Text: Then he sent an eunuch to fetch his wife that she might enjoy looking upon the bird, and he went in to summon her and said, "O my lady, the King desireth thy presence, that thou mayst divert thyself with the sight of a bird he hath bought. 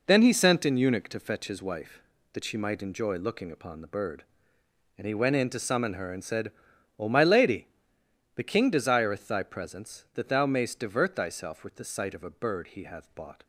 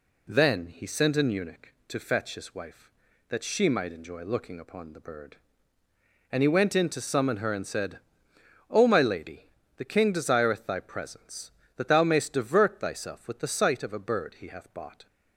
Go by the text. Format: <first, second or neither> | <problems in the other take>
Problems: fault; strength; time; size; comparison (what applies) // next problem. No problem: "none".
second | gets quieter; strong; throughout; 9 dB